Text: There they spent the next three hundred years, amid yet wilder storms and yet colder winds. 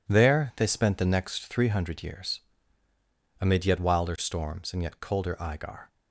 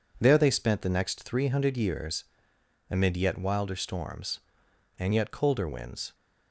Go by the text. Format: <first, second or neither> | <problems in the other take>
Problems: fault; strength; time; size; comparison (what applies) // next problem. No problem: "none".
second | says "igar" for "winds"; at 5.3 s